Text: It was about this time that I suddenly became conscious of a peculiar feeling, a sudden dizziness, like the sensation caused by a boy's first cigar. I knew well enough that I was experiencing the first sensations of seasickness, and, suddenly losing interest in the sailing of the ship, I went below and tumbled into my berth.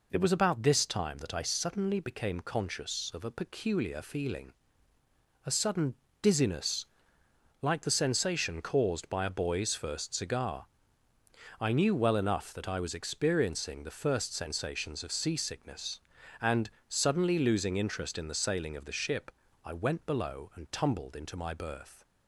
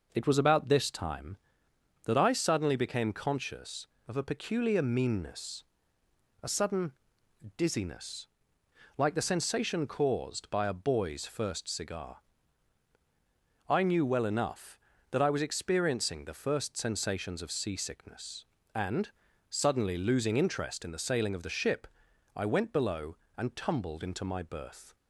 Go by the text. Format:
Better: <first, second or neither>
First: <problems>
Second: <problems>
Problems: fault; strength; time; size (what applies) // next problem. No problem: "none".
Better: first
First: pauses between "sudden" and "dizziness"; slight; at 5.9 s; 0.26 s long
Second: says "meanness" for "feeling"; at 4.8 s // pauses between "sudden" and "dizziness"; noticeable; at 6.9 s; 0.64 s long